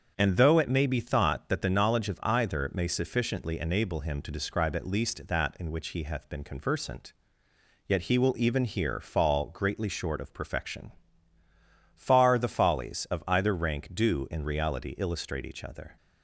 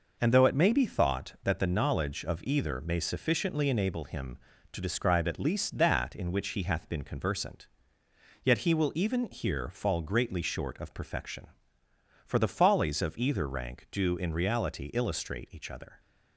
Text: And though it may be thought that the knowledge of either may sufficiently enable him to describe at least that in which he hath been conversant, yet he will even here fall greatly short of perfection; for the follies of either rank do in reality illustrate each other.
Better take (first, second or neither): second